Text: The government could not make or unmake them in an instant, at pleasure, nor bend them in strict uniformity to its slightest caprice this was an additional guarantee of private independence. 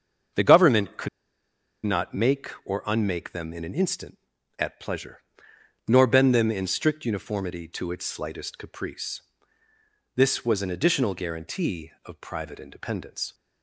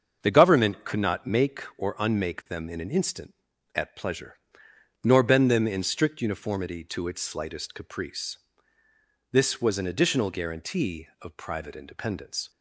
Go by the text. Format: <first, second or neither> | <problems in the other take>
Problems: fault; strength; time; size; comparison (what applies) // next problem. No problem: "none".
second | starts louder than the rest; until 2.1 s; 7 dB; also in the second // pauses between "could" and "not"; noticeable; at 1.0 s; 0.77 s long // pauses between "caprice" and "this"; noticeable; at 9.2 s; 0.94 s long; noticeable in the second